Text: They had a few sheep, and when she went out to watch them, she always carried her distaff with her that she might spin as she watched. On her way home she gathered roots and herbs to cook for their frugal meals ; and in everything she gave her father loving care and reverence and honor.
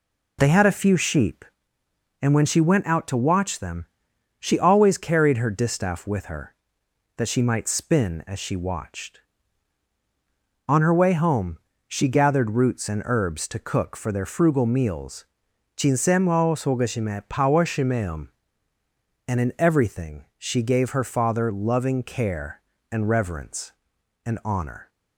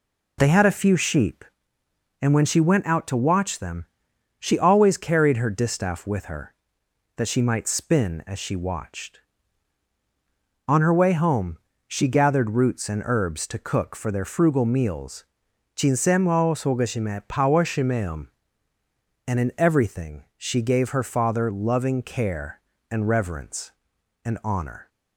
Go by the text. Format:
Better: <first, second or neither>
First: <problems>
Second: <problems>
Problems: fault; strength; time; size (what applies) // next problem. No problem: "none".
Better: neither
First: pauses between "home" and "she"; slight; at 11.5 s; 0.32 s long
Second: pauses between "home" and "she"; slight; at 11.5 s; 0.32 s long